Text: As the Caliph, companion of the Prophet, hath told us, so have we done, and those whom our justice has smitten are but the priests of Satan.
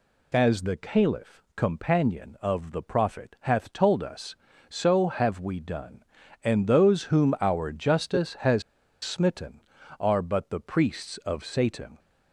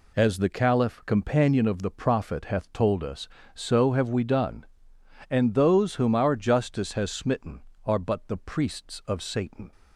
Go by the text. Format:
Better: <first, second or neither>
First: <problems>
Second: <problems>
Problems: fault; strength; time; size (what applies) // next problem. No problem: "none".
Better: second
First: pauses between "has" and "smitten"; at 8.6 s; 0.42 s long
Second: none